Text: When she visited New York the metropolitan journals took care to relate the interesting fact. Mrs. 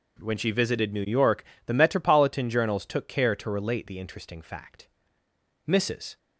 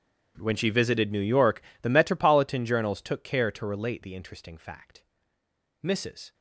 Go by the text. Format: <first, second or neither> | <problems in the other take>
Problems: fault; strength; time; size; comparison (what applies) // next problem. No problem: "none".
first | gets quieter; strong; throughout; 21.5 dB // pauses between "York" and "the"; slight; at 1.6 s; 0.20 s long; slight in the first